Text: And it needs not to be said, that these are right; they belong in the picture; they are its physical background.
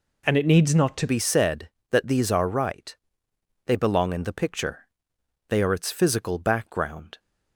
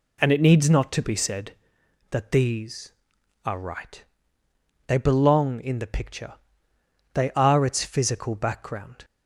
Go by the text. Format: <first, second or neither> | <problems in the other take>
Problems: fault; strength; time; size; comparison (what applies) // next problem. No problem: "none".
second | changes voice at "be"; from 1.0 s on; 6.1 s long